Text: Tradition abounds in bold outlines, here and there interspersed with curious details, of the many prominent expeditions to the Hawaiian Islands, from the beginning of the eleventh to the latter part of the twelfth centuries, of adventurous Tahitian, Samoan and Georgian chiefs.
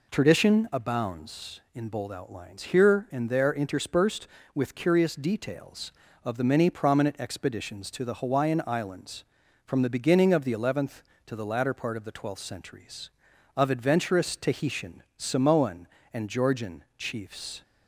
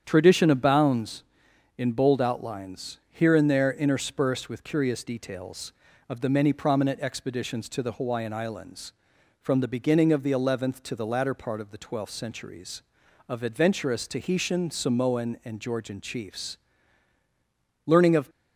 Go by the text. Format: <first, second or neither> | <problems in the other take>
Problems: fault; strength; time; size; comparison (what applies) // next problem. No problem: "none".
first | starts louder than the rest; strong; until 1.0 s; 8.5 dB // goes on to say "Learning of"; slight; from 17.8 s on; 0.42 s long